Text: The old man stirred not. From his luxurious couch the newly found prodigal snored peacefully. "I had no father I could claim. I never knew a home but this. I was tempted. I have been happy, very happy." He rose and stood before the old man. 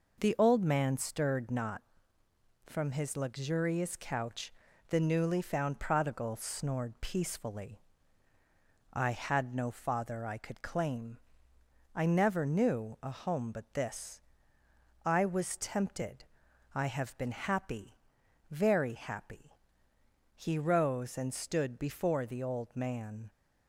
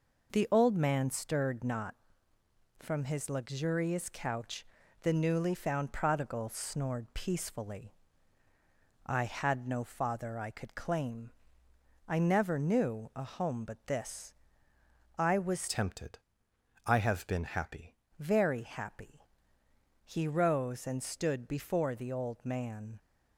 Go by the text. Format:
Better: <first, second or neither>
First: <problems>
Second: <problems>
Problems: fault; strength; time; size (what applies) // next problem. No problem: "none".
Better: first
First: pauses between "couch" and "the"; slight; at 4.5 s; 0.36 s long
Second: pauses between "couch" and "the"; slight; at 4.6 s; 0.36 s long // changes voice from "tempted" to "happy"; from 15.6 to 17.9 s; 2.3 s long